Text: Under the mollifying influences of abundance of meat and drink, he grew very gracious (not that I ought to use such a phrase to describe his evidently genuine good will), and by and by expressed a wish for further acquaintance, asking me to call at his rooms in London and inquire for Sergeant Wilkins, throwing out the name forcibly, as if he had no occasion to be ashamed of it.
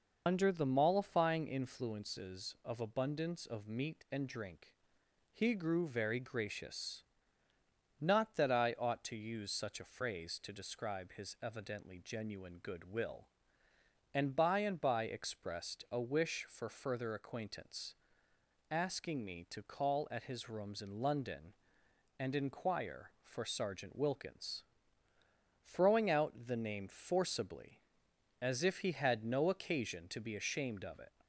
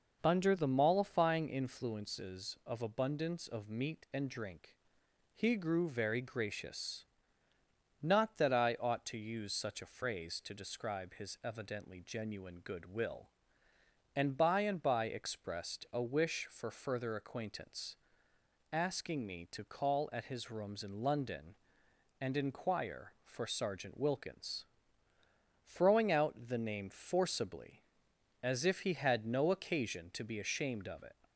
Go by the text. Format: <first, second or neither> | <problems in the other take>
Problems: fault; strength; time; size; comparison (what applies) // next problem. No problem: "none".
second | loses the start of "Under"; at 0.2 s; 85 ms